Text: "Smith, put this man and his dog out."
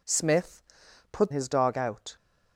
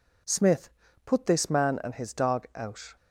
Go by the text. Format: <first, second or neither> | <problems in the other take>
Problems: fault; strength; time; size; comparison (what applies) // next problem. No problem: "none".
second | skips "this man and"; at 1.3 s